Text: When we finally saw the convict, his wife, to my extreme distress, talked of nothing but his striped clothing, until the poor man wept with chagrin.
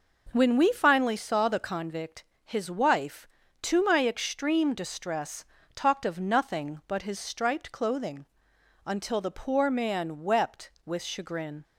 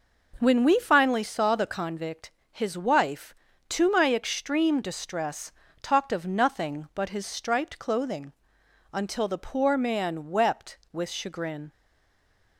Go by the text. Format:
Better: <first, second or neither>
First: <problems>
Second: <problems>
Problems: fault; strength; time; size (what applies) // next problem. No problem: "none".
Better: first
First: none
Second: stays silent after the last word; slight; from 11.7 s on; 0.8 s long